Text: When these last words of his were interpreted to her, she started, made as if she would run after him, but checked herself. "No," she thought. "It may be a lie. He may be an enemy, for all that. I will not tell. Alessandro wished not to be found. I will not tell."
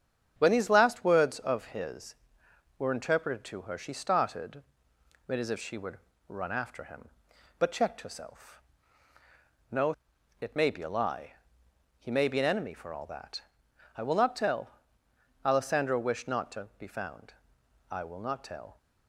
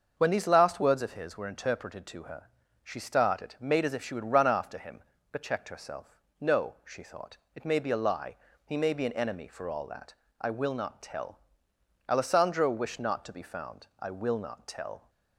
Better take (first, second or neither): second